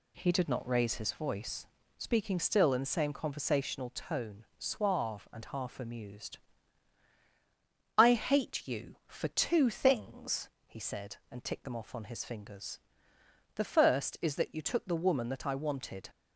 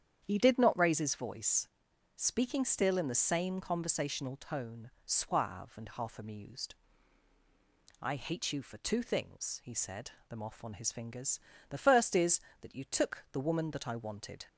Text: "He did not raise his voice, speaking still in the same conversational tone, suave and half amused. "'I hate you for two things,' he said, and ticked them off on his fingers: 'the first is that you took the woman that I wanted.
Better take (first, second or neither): first